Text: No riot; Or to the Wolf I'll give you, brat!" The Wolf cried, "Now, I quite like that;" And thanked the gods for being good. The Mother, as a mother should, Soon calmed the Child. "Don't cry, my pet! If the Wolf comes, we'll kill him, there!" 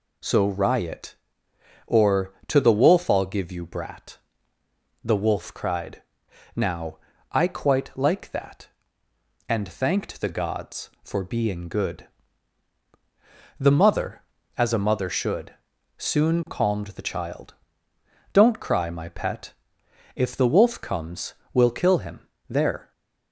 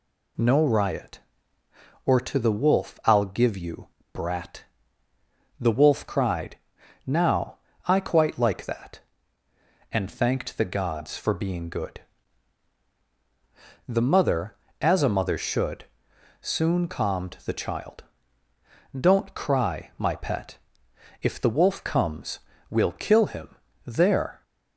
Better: second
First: says "So" for "No"; at 0.2 s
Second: none

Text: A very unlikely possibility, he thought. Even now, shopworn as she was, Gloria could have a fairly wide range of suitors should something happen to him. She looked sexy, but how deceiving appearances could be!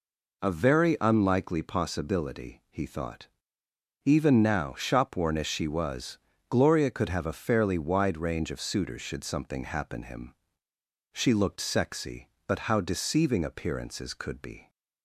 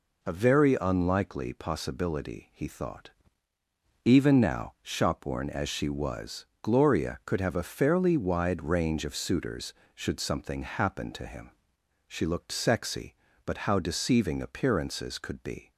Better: second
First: skips "to"; at 10.0 s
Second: none

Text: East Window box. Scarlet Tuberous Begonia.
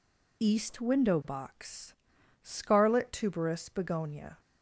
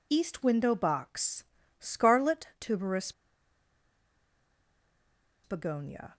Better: first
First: none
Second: pauses between "Tuberous" and "Begonia"; strong; at 3.1 s; 2.3 s long

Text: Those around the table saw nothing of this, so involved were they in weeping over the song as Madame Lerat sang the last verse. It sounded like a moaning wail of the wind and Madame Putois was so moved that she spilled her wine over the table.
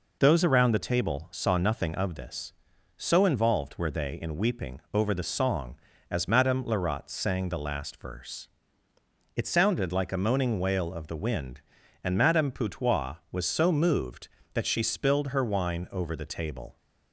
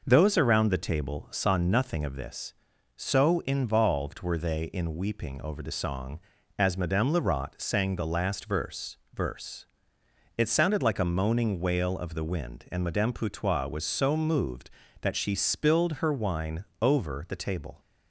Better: first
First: none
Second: says "verse" twice; at 9.1 s // pauses between "wine" and "over"; slight; at 16.6 s; 0.16 s long

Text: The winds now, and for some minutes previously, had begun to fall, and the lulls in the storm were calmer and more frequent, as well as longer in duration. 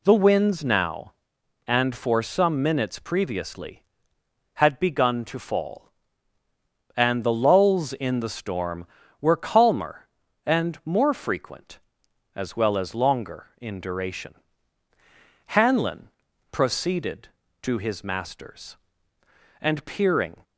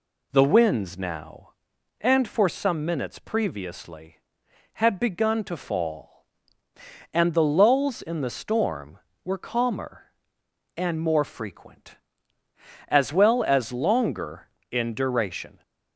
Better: second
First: goes on to say "Hanlon proceeded to his master's and peering"; strong; from 15.4 s on; 4.9 s long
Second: none

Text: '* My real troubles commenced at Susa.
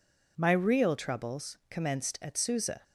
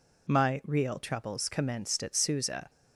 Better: neither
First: none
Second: none

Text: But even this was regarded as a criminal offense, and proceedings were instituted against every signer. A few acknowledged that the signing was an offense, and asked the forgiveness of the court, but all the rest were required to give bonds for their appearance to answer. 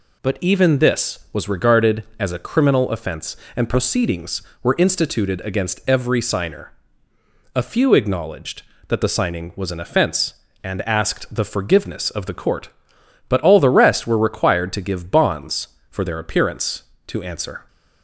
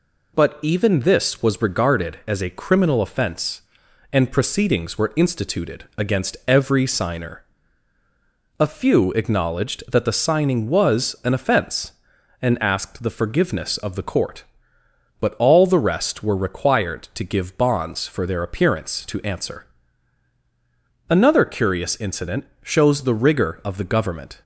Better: first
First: none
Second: goes on to say "Another curious incident shows the rigor of the government"; strong; from 21.0 s on; 3.3 s long

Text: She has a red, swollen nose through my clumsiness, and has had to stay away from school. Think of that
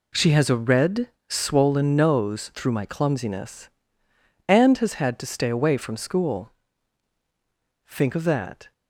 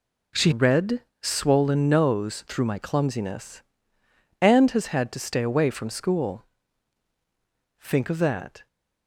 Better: first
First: none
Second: skips "has a"; at 0.5 s

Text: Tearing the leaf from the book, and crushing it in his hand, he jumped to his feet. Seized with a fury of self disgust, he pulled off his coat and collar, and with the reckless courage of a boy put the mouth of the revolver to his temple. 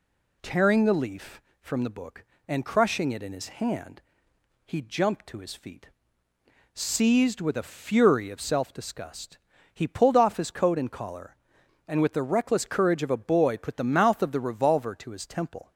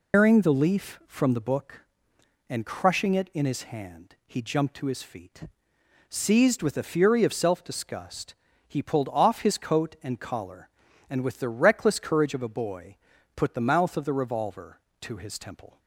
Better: first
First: none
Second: loses the start of "Tearing"; at 0.1 s; 175 ms // pauses between "boy" and "put"; at 12.9 s; 0.40 s long

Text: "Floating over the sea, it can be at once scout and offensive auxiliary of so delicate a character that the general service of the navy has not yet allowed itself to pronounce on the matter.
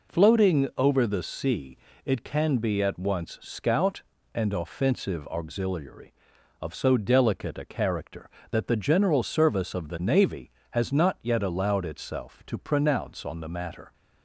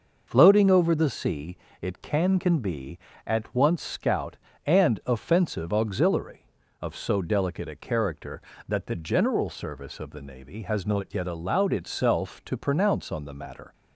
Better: first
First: none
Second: says "can" twice; at 2.3 s

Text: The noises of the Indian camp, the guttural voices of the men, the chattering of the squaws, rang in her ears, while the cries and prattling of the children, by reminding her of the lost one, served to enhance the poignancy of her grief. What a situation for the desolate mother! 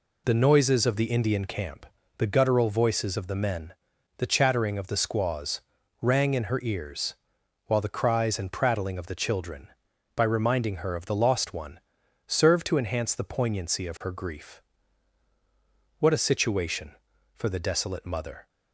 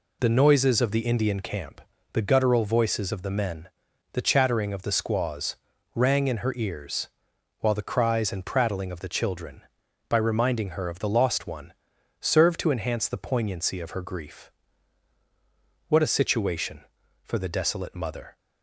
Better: neither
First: none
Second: none

